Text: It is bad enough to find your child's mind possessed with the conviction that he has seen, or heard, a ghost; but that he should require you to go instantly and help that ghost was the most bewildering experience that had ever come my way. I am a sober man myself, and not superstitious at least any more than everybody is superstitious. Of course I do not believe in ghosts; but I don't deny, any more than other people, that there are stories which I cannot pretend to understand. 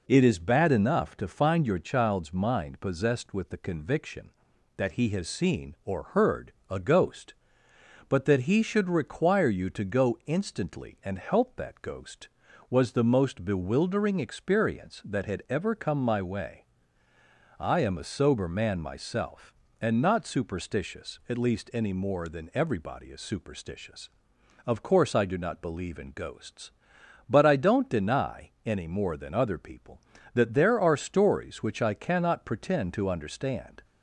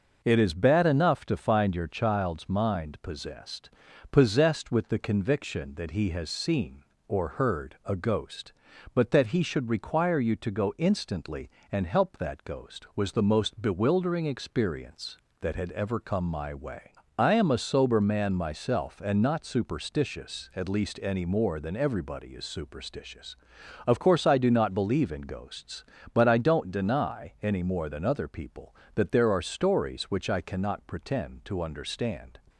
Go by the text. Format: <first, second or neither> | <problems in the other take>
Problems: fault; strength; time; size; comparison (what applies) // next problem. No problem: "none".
first | says "possessed" twice; at 4.1 s